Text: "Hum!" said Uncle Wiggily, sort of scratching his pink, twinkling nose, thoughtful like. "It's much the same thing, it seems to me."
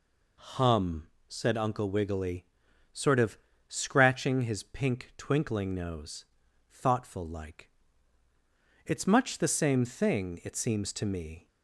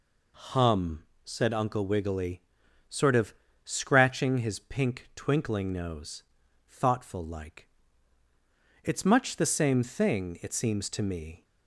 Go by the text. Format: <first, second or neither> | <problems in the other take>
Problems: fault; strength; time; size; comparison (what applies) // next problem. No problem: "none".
neither | pauses between "of" and "scratching"; slight; the same in both